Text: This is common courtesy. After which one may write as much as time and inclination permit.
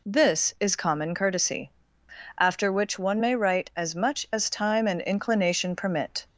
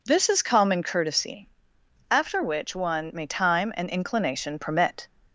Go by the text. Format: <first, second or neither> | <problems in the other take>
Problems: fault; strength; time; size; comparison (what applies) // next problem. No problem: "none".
first | skips "write as much as"; at 3.2 s